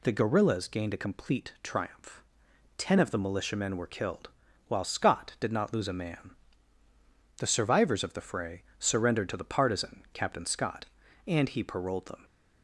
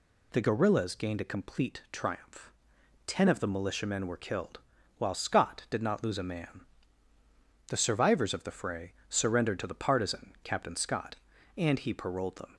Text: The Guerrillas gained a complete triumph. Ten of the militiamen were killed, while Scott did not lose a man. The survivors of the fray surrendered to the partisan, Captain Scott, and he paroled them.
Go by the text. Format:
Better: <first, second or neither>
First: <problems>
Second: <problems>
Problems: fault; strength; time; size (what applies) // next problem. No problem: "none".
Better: neither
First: pauses between "fray" and "surrendered"; slight; at 8.6 s; 0.16 s long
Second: pauses between "fray" and "surrendered"; slight; at 8.9 s; 0.16 s long